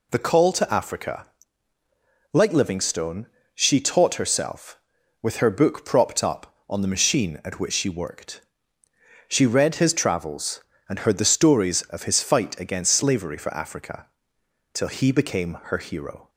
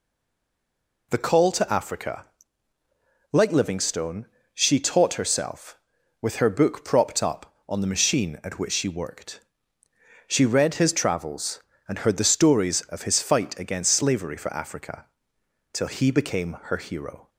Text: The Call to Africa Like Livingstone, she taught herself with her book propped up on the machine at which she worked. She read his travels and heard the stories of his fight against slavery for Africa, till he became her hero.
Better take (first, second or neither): first